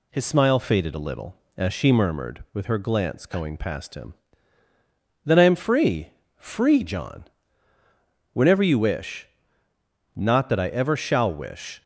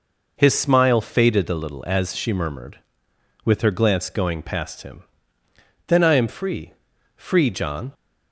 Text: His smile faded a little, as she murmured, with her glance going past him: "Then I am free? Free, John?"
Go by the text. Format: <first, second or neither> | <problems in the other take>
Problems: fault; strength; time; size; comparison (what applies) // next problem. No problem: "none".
second | goes on to say "Whenever you wish Not that I ever shall wish"; strong; from 8.3 s on; 3.5 s long